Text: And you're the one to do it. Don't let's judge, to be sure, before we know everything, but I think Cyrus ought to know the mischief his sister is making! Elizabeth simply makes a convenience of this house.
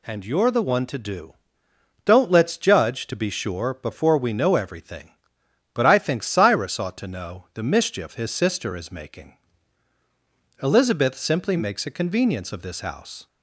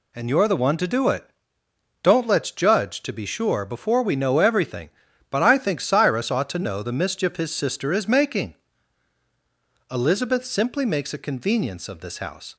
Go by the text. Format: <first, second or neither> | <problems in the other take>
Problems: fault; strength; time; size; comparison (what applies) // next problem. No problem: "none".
second | skips "it"; at 1.6 s